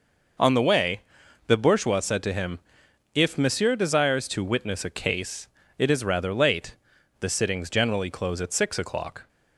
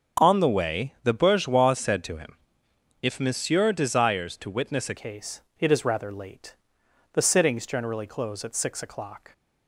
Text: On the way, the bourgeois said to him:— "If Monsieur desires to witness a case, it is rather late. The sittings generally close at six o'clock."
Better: first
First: none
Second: starts louder than the rest; until 1.3 s; 6.5 dB // changes voice at "case"; from 4.9 s on; 4.4 s long

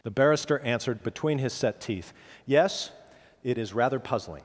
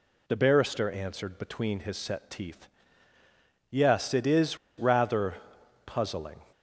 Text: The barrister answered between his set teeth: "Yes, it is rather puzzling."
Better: first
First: none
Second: pauses between "is" and "rather"; slight; at 4.5 s; 0.21 s long // pauses between "rather" and "puzzling"; noticeable; at 5.3 s; 0.50 s long

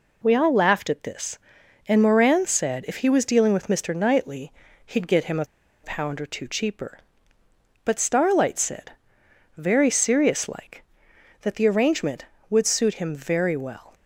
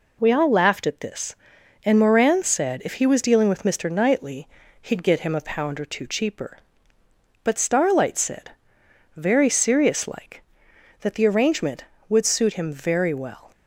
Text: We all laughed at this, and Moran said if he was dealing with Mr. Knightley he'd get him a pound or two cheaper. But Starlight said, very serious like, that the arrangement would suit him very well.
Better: second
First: pauses between "Knightley" and "he'd"; slight; at 4.5 s; 0.34 s long // pauses between "a" and "pound"; at 5.4 s; 0.38 s long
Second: pauses between "Knightley" and "he'd"; slight; at 4.4 s; 0.34 s long

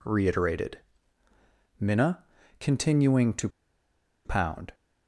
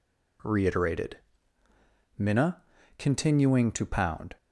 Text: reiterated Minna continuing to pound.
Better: second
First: pauses between "reiterated" and "Minna"; at 0.7 s; 1.0 s long // pauses between "Minna" and "continuing"; slight; at 2.2 s; 0.34 s long // pauses between "to" and "pound"; noticeable; at 3.4 s; 0.77 s long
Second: pauses between "reiterated" and "Minna"; at 1.1 s; 1.0 s long // pauses between "Minna" and "continuing"; slight; at 2.6 s; 0.34 s long

